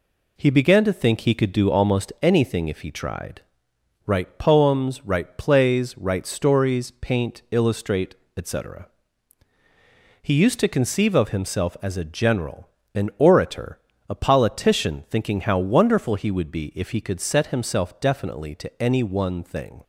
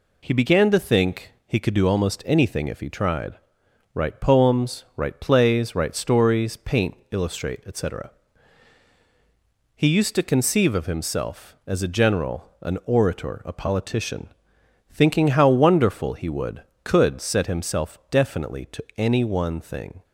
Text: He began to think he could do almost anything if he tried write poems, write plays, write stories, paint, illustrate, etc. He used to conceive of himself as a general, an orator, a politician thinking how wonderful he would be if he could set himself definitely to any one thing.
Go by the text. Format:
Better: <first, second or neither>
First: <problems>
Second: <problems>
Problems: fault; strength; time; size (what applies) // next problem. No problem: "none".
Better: first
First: pauses between "tried" and "write"; noticeable; at 3.4 s; 0.64 s long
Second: pauses between "tried" and "write"; noticeable; at 3.3 s; 0.60 s long // pauses between "politician" and "thinking"; noticeable; at 14.2 s; 0.62 s long // skips "be if he"; at 16.7 s